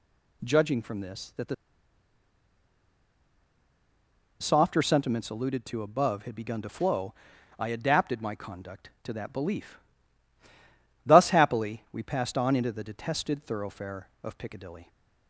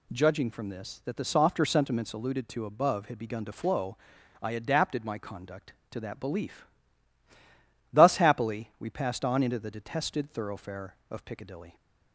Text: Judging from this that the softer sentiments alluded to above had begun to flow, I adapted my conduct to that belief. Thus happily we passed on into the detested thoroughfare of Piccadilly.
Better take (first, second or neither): second